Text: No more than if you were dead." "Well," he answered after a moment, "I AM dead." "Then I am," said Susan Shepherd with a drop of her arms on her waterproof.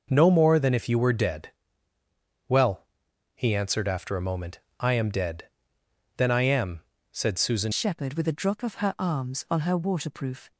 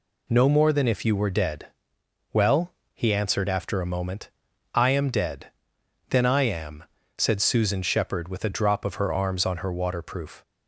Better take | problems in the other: second | changes voice at "Shepherd"; from 7.7 s on; 2.8 s long

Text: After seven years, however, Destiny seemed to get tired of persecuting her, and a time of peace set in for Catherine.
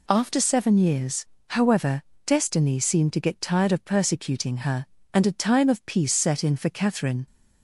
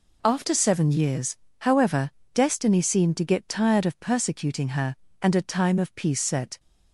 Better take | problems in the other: first | stops before "in for Catherine"; at 6.5 s

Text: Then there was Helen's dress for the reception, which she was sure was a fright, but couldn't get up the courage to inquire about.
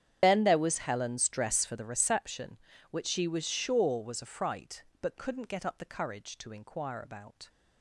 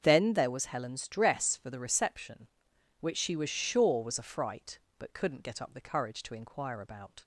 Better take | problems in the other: second | loses the start of "Then"; at 0.2 s; 40 ms // starts louder than the rest; strong; until 1.2 s; 9 dB; also in the second

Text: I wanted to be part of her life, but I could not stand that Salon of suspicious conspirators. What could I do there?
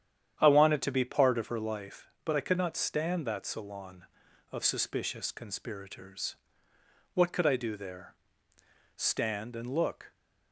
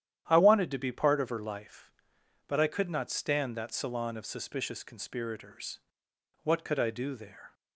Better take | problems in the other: second | starts louder than the rest; strong; until 1.3 s; 9.5 dB; strong in the second // goes on to say "Stand and look"; noticeable; from 8.9 s on; 1.1 s long

